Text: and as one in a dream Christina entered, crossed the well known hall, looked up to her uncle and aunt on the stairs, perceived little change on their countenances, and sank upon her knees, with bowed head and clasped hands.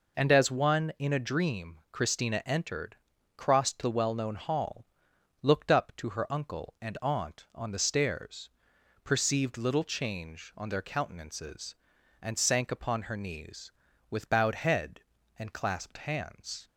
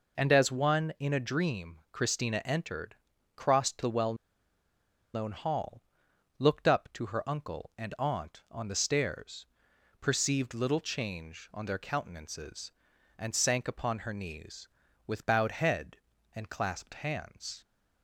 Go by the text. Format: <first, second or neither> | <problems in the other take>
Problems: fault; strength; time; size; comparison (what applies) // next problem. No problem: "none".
first | pauses between "well" and "known"; at 4.1 s; 0.99 s long